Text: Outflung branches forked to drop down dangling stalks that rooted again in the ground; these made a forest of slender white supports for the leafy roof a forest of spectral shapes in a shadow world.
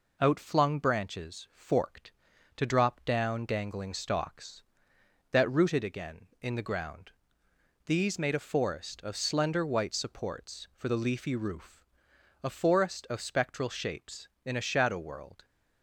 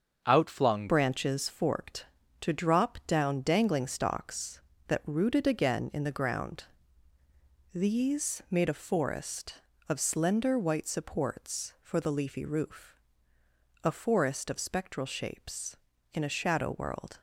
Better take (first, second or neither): first